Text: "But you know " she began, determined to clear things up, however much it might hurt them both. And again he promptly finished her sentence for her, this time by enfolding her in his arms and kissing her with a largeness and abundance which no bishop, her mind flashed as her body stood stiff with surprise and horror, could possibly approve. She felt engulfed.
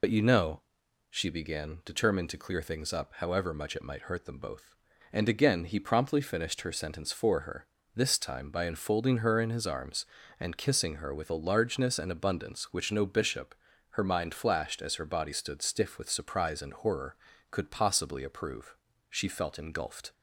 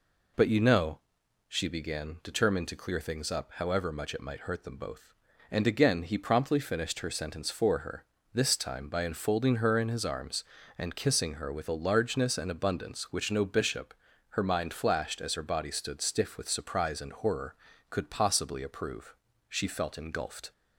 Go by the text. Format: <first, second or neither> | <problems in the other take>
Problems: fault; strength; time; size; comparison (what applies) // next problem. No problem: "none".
second | loses the start of "But"; at 0.0 s; 60 ms